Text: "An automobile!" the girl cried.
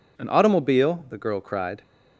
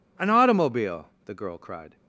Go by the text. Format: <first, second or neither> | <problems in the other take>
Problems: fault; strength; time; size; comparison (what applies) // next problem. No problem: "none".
neither | none